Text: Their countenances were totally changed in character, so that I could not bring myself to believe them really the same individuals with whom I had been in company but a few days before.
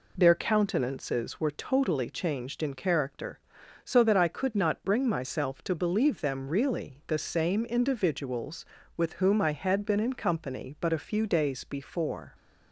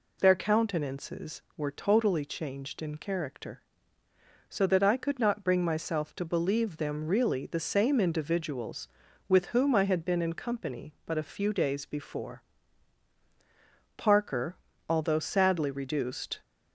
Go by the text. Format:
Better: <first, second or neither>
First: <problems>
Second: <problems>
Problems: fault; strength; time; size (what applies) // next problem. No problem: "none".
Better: first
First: none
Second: goes on to say "Parker although sadly reduced"; strong; from 13.9 s on; 2.4 s long